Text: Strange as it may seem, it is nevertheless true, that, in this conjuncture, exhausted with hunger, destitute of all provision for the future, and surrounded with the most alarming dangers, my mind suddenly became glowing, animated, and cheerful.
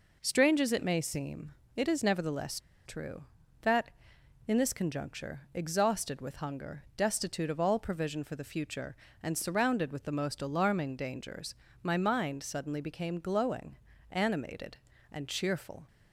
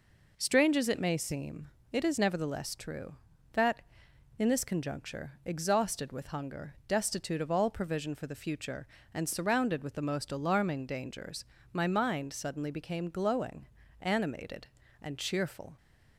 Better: second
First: pauses between "nevertheless" and "true"; slight; at 2.5 s; 0.26 s long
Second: none

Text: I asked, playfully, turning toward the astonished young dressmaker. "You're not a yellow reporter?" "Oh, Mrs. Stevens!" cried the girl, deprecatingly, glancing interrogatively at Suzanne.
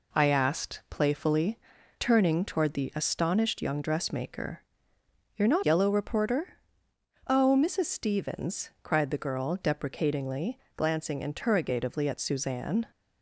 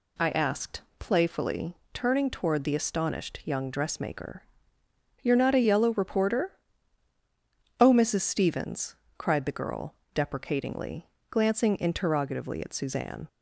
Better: second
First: skips "a"; at 5.6 s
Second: none

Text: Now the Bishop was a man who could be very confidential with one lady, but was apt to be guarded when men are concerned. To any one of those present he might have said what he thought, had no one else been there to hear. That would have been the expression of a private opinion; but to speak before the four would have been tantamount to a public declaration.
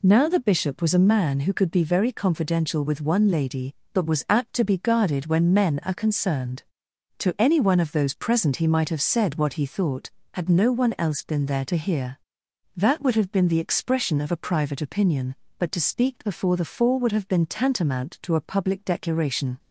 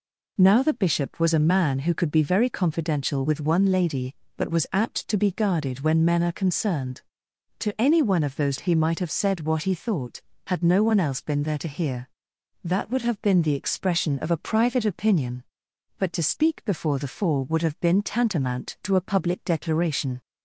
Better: first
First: none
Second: skips "present"; at 8.5 s

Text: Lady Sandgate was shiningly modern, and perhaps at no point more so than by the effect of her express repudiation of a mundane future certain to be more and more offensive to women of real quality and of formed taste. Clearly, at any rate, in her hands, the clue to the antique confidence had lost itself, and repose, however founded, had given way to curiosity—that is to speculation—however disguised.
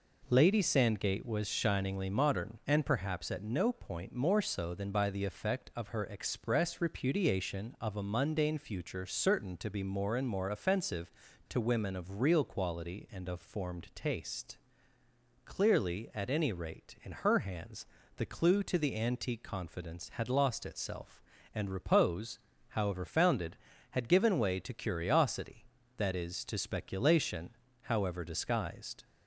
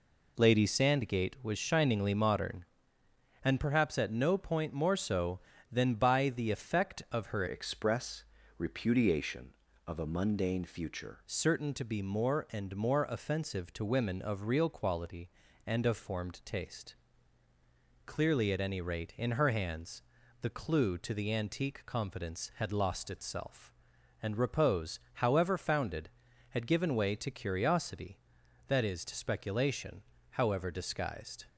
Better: first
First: none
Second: changes voice from "express" to "future"; from 7.4 to 11.2 s; 3.8 s long // pauses between "express" and "repudiation"; slight; at 8.2 s; 0.34 s long

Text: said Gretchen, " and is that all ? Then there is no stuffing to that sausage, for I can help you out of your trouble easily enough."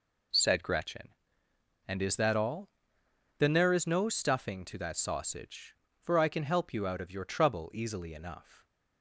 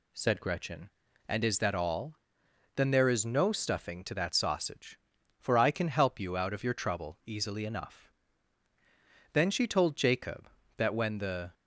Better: first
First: none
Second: goes on to say "Then she told Jacob that when the"; strong; from 9.3 s on; 2.2 s long

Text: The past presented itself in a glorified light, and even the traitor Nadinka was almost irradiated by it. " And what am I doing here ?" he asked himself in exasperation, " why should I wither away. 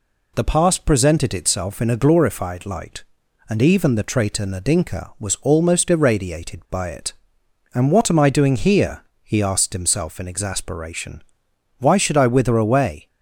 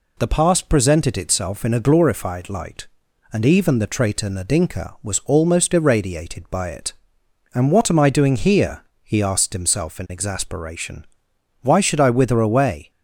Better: neither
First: none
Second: none

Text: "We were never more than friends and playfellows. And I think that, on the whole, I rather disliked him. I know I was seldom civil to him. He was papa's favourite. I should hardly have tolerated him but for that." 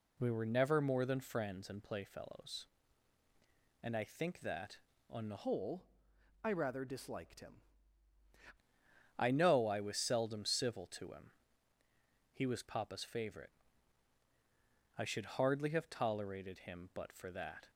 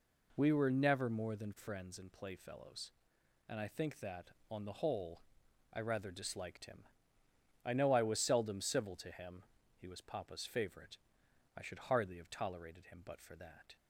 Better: second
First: changes voice from "whole" to "him"; from 5.4 to 7.6 s; 2.2 s long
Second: none

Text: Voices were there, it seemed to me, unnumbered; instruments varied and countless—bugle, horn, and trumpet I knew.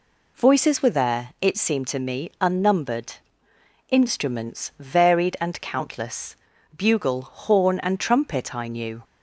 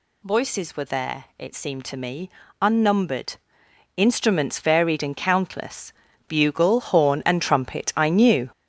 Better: first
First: none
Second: gets louder; strong; throughout; 7.5 dB

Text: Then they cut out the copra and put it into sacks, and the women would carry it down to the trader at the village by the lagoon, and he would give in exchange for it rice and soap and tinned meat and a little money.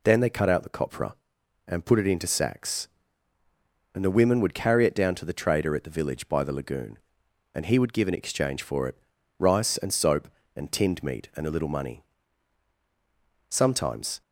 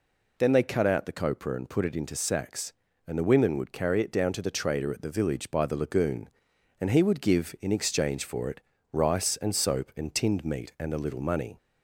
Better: second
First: pauses between "it" and "rice"; at 8.9 s; 0.40 s long // goes on to say "Sometimes"; noticeable; from 13.4 s on; 0.72 s long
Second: pauses between "it" and "rice"; slight; at 8.6 s; 0.32 s long

